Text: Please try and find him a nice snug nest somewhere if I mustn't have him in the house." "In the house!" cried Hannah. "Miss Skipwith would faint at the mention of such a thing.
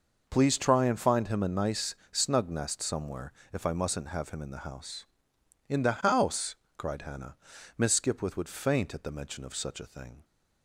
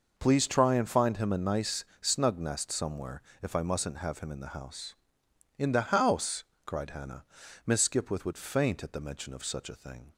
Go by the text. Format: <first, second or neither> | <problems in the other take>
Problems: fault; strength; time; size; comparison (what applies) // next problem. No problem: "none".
neither | pauses between "nice" and "snug"; slight; the same in both // pauses between "somewhere" and "if"; slight; the same in both